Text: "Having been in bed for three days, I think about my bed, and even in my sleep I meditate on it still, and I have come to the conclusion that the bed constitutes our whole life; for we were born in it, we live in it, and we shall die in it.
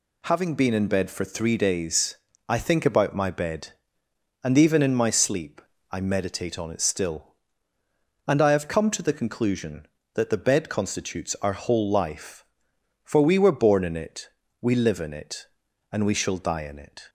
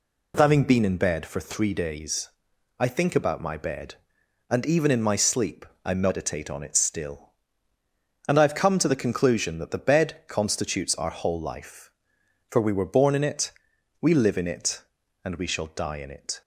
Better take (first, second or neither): neither